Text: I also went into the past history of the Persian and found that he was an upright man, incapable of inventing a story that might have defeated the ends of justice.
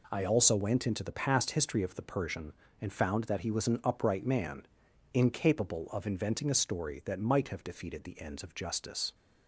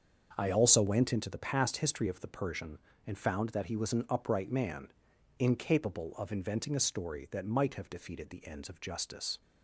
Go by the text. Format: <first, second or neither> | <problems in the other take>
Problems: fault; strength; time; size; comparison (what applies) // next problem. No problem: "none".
first | starts louder than the rest; until 1.2 s; 6.5 dB